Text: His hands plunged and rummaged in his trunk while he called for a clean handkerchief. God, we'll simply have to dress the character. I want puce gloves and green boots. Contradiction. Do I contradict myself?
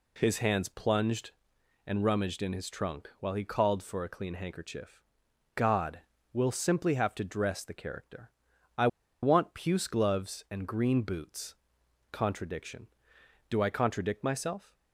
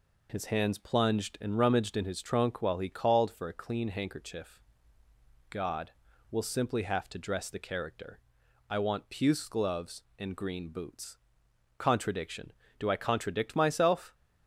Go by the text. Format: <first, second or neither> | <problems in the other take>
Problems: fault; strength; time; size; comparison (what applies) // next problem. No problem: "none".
second | pauses between "I" and "want"; slight; at 8.8 s; 0.35 s long